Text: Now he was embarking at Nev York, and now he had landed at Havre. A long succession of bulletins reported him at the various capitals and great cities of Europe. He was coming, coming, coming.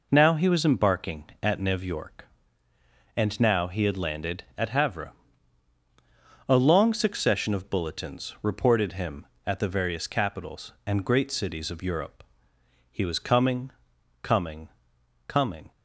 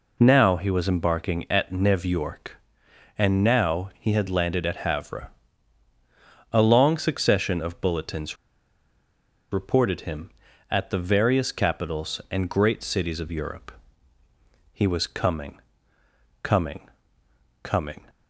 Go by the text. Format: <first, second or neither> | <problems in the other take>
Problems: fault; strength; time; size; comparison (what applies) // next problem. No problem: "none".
first | pauses between "bulletins" and "reported"; at 8.3 s; 1.1 s long